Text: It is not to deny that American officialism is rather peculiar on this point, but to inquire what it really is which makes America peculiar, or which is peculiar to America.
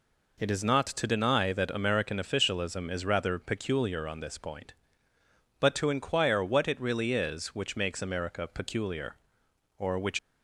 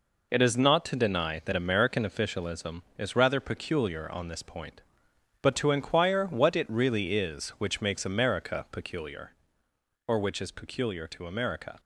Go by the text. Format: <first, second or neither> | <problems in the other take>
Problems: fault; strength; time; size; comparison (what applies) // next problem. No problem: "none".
second | stops before "is peculiar to America"; at 10.1 s